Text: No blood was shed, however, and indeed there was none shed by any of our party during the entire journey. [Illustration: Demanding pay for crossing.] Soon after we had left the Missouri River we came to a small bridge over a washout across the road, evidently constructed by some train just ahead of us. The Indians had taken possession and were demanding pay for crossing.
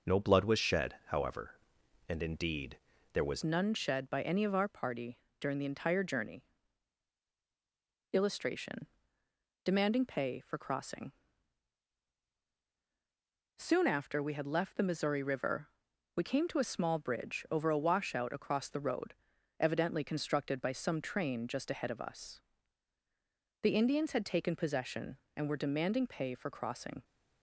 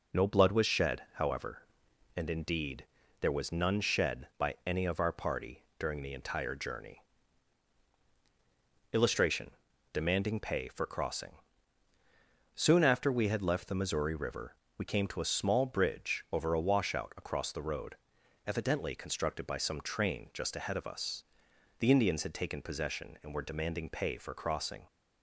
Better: second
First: pauses between "indeed" and "there"; at 2.7 s; 0.38 s long // changes voice at "none"; from 3.4 s on; 23.6 s long // pauses between "party" and "during"; slight; at 5.1 s; 0.22 s long // pauses between "River" and "we"; noticeable; at 15.6 s; 0.48 s long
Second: pauses between "indeed" and "there"; at 2.8 s; 0.38 s long // pauses between "party" and "during"; slight; at 5.6 s; 0.16 s long // pauses between "River" and "we"; slight; at 14.5 s; 0.20 s long

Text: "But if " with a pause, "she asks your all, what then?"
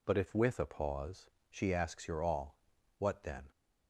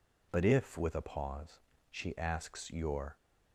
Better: first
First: none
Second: stops before "all what then"; at 3.1 s

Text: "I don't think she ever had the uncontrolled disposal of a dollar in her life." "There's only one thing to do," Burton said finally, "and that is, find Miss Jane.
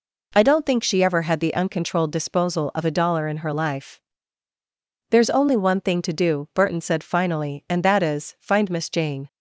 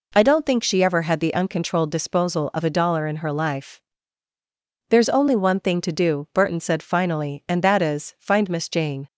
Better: neither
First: none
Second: none

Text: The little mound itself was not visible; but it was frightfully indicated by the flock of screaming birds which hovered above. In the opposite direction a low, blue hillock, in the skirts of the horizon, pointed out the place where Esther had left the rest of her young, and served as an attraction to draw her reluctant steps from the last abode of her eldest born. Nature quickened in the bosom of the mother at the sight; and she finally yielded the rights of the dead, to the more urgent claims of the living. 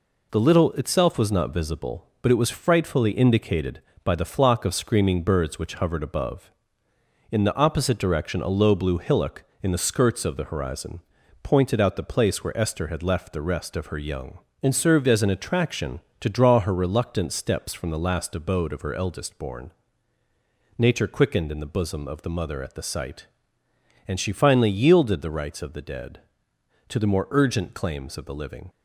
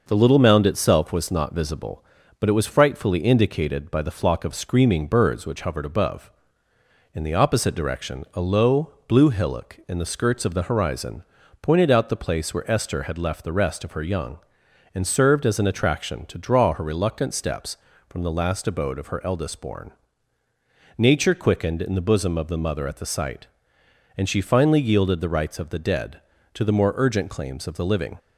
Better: second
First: skips "mound"; at 0.7 s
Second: none

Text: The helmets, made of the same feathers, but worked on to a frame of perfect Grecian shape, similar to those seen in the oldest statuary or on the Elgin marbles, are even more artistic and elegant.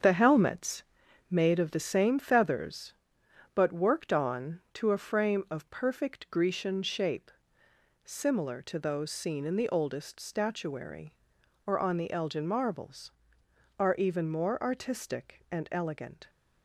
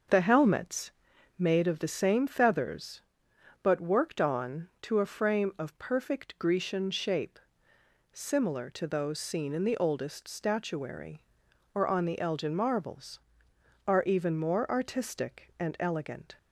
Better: second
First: gets quieter; strong; throughout; 7.5 dB // starts louder than the rest; strong; until 1.4 s; 7 dB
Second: starts louder than the rest; until 1.5 s; 6.5 dB

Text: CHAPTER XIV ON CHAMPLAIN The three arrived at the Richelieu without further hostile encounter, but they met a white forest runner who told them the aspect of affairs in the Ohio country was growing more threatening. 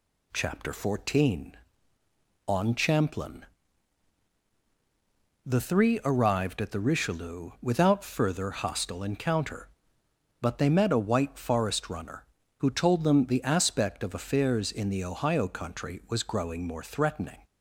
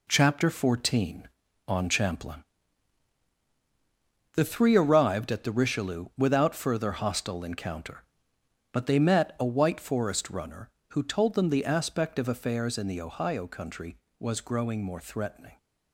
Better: neither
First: pauses between "CHAMPLAIN" and "The"; strong; at 3.4 s; 2.0 s long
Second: pauses between "CHAMPLAIN" and "The"; strong; at 2.4 s; 1.9 s long

